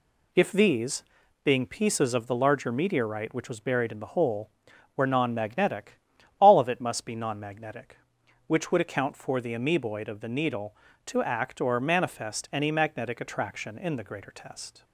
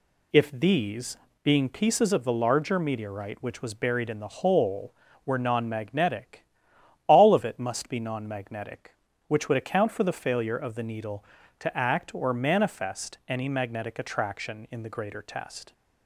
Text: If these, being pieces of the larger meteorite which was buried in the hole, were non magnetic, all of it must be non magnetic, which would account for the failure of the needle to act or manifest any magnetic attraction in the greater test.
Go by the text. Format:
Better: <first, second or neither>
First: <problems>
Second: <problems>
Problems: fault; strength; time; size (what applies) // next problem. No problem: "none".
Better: second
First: says "amoeboid" for "failure"; at 9.5 s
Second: none